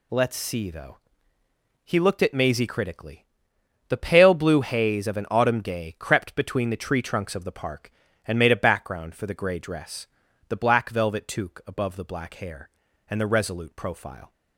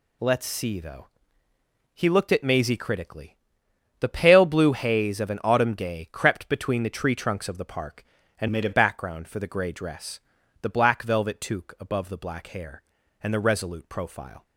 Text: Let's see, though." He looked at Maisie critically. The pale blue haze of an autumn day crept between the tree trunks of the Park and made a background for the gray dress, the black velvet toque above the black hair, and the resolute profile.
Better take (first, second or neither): first